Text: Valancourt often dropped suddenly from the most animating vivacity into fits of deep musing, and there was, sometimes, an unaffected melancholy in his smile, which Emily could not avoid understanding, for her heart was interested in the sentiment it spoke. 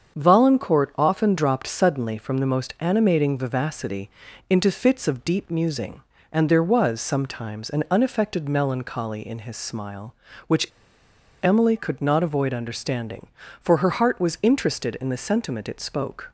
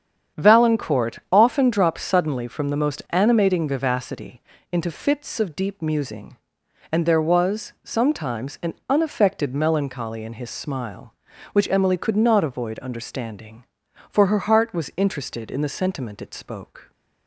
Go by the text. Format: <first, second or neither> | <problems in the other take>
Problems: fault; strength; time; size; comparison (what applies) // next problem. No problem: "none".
second | starts louder than the rest; strong; until 1.2 s; 7 dB; strong in the second // pauses between "vivacity" and "into"; at 4.0 s; 0.40 s long; slight in the second // pauses between "which" and "Emily"; noticeable; at 10.6 s; 0.78 s long